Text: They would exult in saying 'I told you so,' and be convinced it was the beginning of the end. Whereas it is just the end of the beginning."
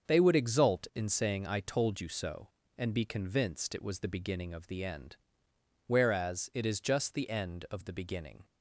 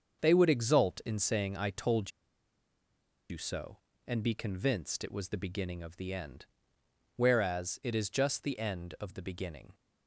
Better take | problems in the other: first | starts louder than the rest; until 1.2 s; 7 dB; also in the first // pauses between "told" and "you"; at 2.1 s; 1.1 s long

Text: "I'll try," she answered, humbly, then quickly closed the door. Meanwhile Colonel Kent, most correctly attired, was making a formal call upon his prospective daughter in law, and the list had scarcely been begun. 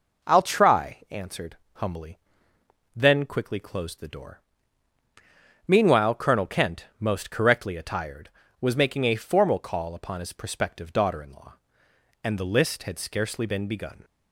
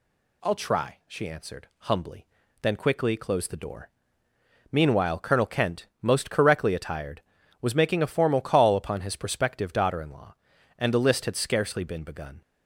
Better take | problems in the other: second | skips "she"; at 1.0 s

